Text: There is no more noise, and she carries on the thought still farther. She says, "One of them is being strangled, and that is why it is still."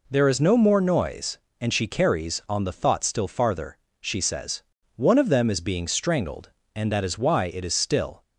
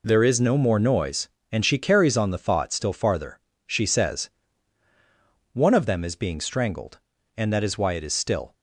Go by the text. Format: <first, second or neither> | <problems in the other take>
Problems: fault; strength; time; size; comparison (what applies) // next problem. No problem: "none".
neither | none